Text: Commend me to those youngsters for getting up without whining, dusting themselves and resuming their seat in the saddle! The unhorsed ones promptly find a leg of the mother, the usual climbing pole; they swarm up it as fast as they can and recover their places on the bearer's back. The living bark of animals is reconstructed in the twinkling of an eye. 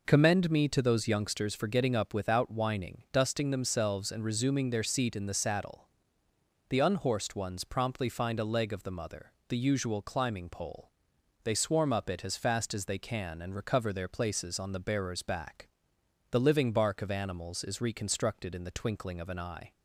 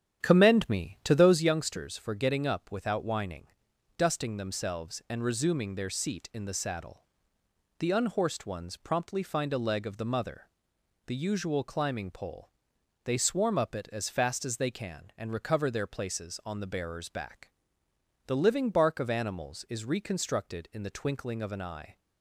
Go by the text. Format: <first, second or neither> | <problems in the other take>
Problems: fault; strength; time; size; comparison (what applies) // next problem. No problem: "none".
first | starts louder than the rest; strong; until 1.4 s; 9.5 dB